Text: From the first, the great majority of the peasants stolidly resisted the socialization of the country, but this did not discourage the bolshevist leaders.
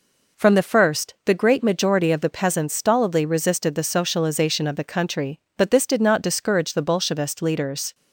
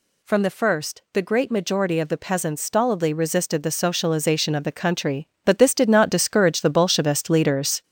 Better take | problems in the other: first | gets louder; noticeable; throughout; 6 dB

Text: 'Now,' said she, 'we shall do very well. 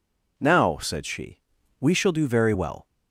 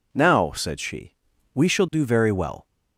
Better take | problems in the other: neither | none

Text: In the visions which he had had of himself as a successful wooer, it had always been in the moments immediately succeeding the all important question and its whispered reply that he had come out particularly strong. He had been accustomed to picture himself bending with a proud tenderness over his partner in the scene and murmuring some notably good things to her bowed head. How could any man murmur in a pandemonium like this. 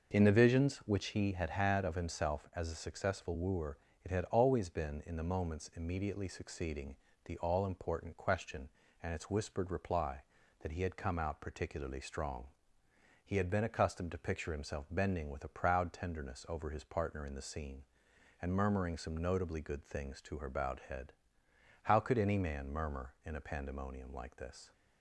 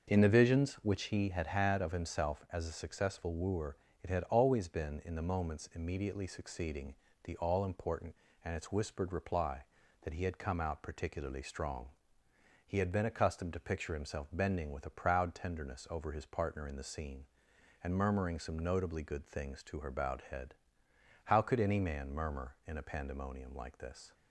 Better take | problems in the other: first | starts louder than the rest; until 1.1 s; 6.5 dB // pauses between "succeeding" and "the"; slight; at 6.9 s; 0.30 s long; slight in the first // skips "question"; at 8.3 s

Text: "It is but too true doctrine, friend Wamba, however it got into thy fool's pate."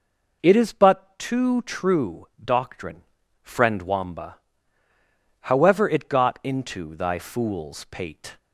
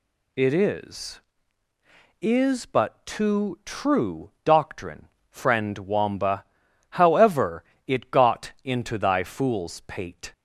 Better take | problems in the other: first | says "is" twice; at 2.2 s // pauses between "true" and "doctrine"; slight; at 4.3 s; 0.16 s long; slight in the first // pauses between "however" and "it"; slight; at 7.6 s; 0.22 s long

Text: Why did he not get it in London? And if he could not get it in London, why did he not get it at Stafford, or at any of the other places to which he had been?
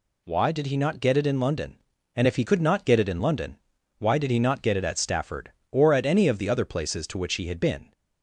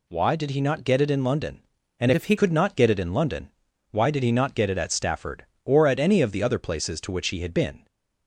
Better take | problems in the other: first | changes voice from "if" to "he"; from 2.1 to 2.3 s; 0.2 s long

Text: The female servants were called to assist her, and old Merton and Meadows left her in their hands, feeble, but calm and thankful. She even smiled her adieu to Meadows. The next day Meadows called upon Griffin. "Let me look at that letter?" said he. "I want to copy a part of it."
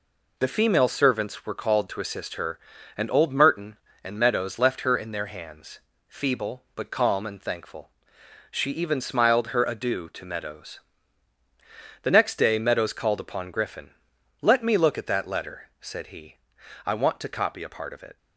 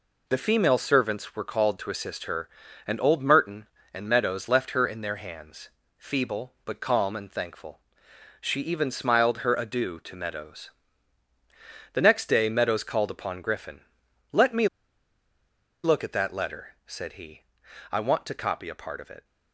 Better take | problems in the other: first | pauses between "me" and "look"; at 14.6 s; 1.1 s long

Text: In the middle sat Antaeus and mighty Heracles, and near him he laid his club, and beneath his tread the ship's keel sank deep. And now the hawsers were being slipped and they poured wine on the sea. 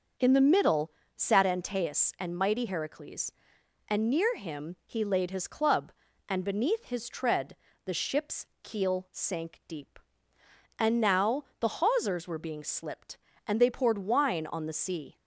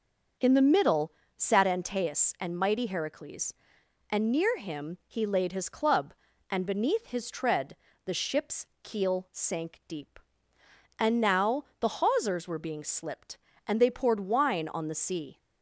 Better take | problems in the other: neither | starts louder than the rest; noticeable; the same in both // pauses between "middle" and "sat"; slight; the same in both // pauses between "tread" and "the"; slight; the same in both // pauses between "ship's" and "keel"; slight; the same in both // pauses between "now" and "the"; slight; the same in both

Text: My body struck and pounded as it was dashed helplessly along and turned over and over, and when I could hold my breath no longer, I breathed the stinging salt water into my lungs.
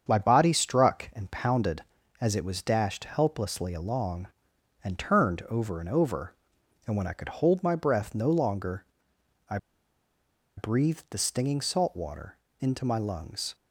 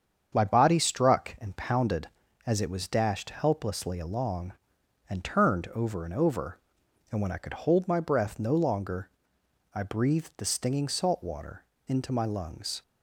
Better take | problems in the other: second | starts louder than the rest; strong; until 1.0 s; 7.5 dB; strong in the second // pauses between "I" and "breathed"; at 9.5 s; 1.0 s long // pauses between "water" and "into"; slight; at 12.3 s; 0.22 s long; slight in the second

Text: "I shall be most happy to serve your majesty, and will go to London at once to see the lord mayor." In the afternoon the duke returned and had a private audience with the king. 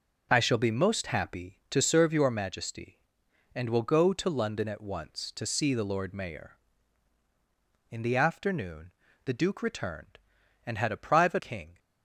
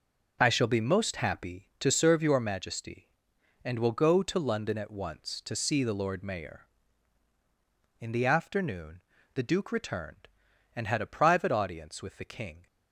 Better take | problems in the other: second | pauses between "afternoon" and "the"; slight; at 8.9 s; 0.32 s long; slight in the second // skips "audience with the"; at 11.3 s

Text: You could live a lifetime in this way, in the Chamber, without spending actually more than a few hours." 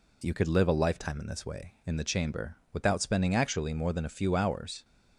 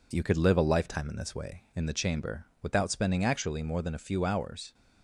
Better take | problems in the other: first | gets quieter; slight; throughout; 2.5 dB

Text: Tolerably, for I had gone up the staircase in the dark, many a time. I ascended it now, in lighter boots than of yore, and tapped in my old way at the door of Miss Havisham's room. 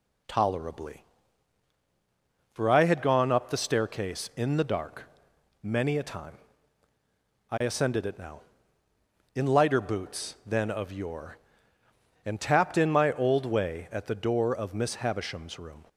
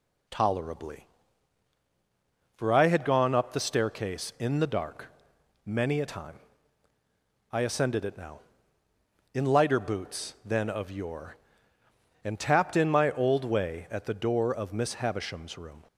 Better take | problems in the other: neither | none

